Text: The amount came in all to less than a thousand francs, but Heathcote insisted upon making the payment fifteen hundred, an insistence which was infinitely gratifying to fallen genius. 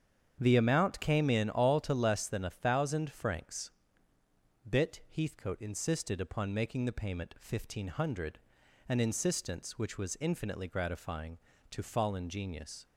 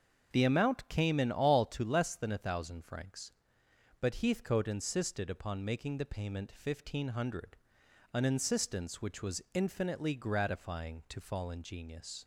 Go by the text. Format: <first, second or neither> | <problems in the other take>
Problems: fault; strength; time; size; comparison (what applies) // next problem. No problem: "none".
second | starts louder than the rest; strong; until 1.4 s; 8 dB; also in the second // says "bit" for "but"; at 4.6 s